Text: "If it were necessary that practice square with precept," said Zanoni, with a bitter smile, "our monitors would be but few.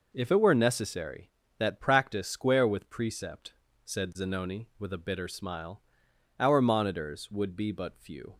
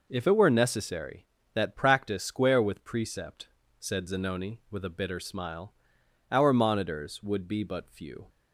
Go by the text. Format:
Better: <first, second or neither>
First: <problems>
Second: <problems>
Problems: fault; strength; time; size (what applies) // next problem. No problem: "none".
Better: neither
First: none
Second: none